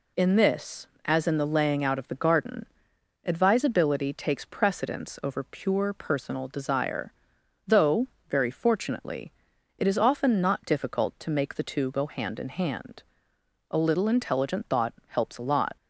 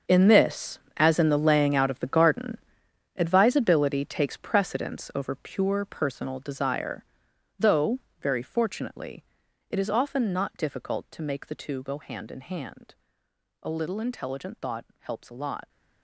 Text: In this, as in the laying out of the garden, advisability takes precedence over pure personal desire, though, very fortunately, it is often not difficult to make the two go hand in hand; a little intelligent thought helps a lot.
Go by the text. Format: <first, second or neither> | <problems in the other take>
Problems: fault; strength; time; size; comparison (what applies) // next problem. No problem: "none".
first | gets quieter; strong; throughout; 14.5 dB